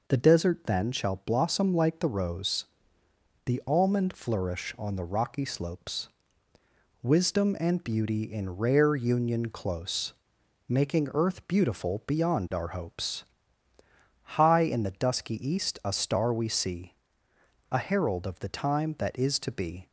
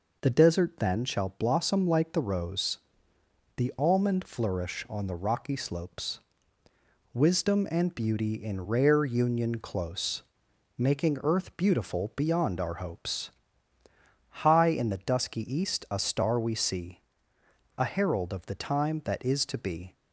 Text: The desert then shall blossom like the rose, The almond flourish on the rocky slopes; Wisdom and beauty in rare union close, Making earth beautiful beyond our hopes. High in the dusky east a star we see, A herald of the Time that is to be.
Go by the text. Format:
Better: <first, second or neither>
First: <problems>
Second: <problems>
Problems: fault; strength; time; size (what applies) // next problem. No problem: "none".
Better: neither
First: none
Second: none